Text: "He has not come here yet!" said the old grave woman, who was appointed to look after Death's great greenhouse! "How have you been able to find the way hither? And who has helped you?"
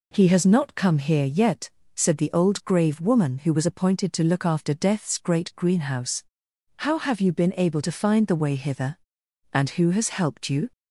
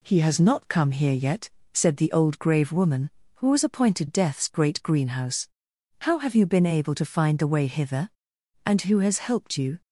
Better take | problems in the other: first | skips "to look after"; at 4.0 s

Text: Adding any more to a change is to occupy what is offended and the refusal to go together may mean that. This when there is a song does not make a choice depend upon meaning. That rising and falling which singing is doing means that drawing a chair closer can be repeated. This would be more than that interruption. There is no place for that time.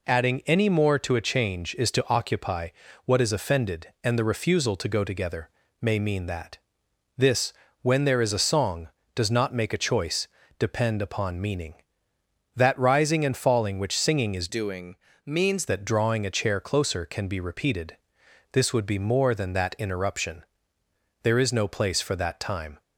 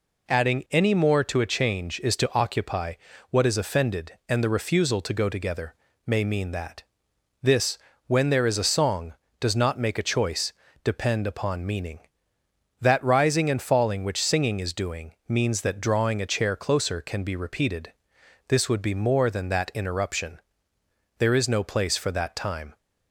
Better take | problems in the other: second | pauses between "occupy" and "what"; slight; at 2.6 s; 0.34 s long; slight in the second // pauses between "together" and "may"; slight; at 5.4 s; 0.30 s long; slight in the second // pauses between "This" and "when"; slight; at 7.5 s; 0.30 s long; slight in the second // pauses between "choice" and "depend"; slight; at 10.2 s; 0.30 s long; slight in the second // changes voice from "doing" to "means"; from 14.4 to 15.6 s; 1.2 s long // pauses between "doing" and "means"; slight; at 14.9 s; 0.32 s long; slight in the second

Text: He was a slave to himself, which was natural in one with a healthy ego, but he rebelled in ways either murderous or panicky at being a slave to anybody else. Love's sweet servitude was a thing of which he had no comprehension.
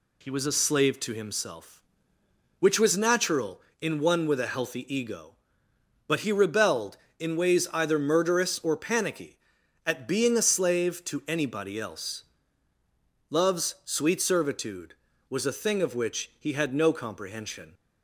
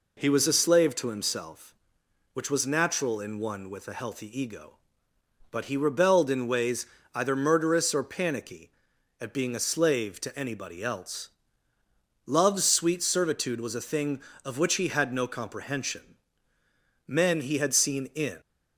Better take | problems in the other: first | pauses between "ways" and "either"; slight; at 6.8 s; 0.28 s long // goes on to say "Men he had seen in"; from 17.0 s on; 1.3 s long

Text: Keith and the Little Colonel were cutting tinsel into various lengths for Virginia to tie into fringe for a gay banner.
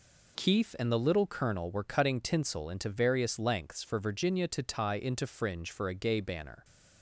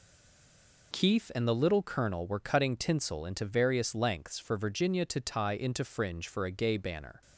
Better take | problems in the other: first | stays silent before the first word; slight; until 0.9 s; 0.9 s long

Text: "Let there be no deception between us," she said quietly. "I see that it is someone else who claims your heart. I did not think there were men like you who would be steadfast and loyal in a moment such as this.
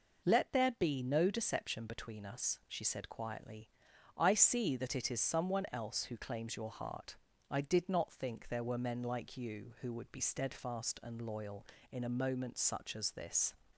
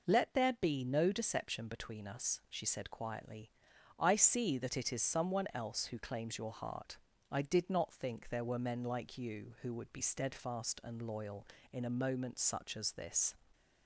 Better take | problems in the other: neither | none

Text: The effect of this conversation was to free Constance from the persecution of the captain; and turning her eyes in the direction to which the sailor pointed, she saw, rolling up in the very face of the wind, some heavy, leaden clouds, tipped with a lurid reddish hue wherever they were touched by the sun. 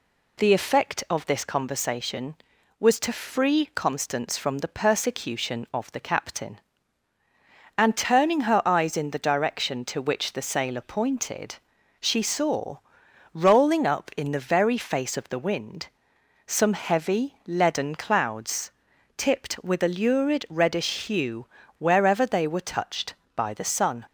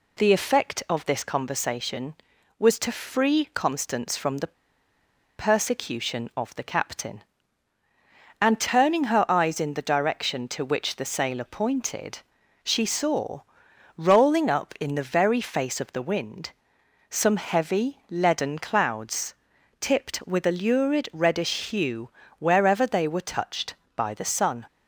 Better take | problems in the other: first | pauses between "the" and "persecution"; noticeable; at 4.5 s; 0.86 s long // pauses between "hue" and "wherever"; slight; at 22.0 s; 0.28 s long; slight in the first

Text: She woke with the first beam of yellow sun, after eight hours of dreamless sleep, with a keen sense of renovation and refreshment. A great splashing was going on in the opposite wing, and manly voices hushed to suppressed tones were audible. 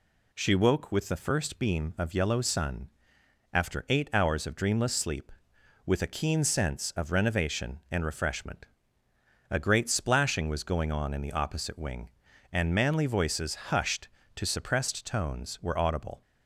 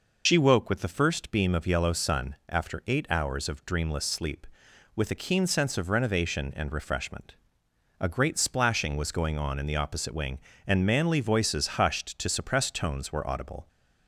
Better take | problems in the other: first | loses the start of "She"; at 0.2 s; 70 ms

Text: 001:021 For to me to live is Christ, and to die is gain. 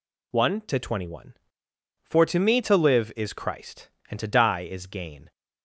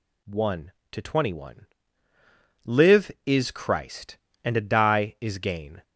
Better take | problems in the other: first | skips "For to me to"; at 2.1 s

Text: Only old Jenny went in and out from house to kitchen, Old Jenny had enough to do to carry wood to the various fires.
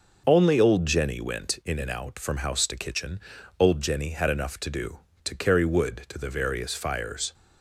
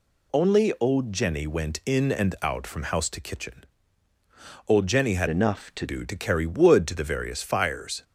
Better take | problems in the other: first | changes voice from "enough" to "to"; from 5.2 to 5.8 s; 0.6 s long

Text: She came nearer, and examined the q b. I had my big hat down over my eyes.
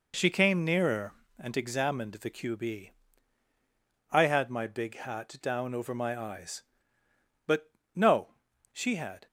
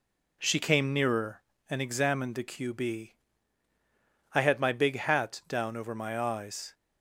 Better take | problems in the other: second | goes on to say "But no she had"; strong; from 7.4 s on; 1.8 s long

